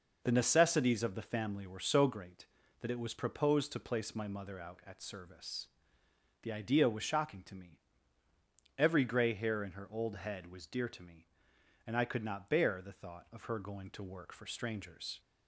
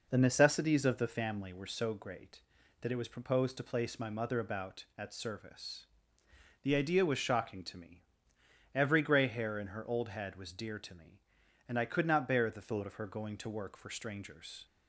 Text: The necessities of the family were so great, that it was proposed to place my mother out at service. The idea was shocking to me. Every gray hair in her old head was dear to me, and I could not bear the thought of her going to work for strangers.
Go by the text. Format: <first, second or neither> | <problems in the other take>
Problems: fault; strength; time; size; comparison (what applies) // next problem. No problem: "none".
first | says "about" for "out"; at 4.3 s